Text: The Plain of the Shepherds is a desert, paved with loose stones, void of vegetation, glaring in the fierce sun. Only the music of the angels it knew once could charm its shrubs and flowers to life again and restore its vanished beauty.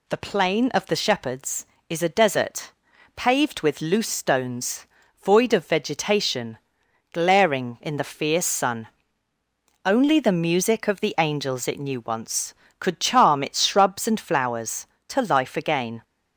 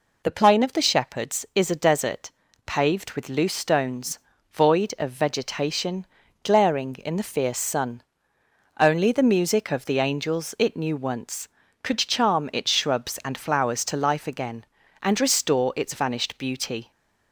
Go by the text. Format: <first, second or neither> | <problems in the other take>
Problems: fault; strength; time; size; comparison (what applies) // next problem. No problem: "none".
second | stops before "and restore its vanished beauty"; at 16.0 s